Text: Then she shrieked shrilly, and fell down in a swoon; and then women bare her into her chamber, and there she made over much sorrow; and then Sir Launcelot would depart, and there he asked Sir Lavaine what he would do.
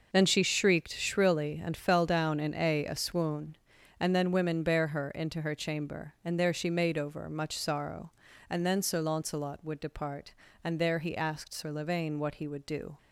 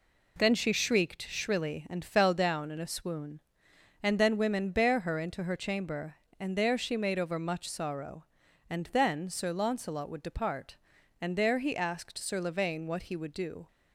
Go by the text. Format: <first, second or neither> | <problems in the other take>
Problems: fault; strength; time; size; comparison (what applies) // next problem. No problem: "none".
second | says "a" twice; at 2.8 s